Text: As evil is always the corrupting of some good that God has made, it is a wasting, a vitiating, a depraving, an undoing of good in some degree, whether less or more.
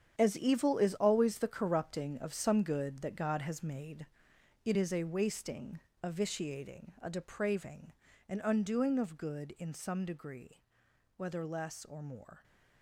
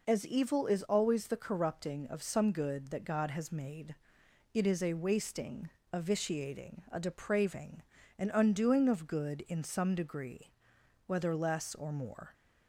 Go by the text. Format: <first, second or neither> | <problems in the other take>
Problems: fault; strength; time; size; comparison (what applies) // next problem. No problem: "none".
second | gets quieter; strong; throughout; 11.5 dB